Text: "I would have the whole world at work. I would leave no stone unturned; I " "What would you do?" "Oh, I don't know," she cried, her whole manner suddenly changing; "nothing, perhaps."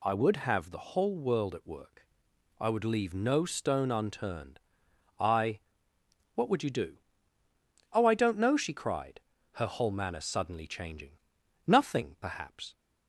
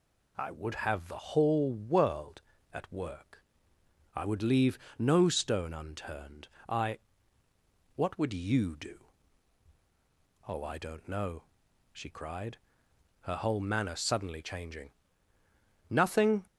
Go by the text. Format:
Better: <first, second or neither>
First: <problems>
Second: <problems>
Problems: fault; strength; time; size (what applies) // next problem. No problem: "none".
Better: first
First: none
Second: pauses between "leave" and "no"; slight; at 4.7 s; 0.22 s long // stops before "perhaps"; at 16.4 s